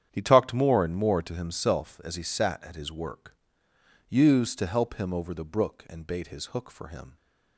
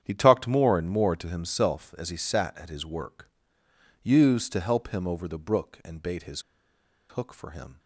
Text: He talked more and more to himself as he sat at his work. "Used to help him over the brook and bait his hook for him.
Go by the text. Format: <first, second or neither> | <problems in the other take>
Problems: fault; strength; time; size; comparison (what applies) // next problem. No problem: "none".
first | starts louder than the rest; strong; until 1.0 s; 9.5 dB; strong in the first // pauses between "his" and "hook"; noticeable; at 6.4 s; 0.67 s long